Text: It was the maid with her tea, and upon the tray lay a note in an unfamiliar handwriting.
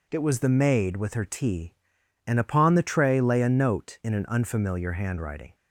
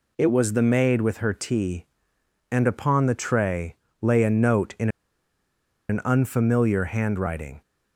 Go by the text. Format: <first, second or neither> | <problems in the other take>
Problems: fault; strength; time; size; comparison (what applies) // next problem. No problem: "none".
first | pauses between "tray" and "lay"; slight; at 3.7 s; 0.26 s long // pauses between "in" and "an"; at 4.8 s; 1.0 s long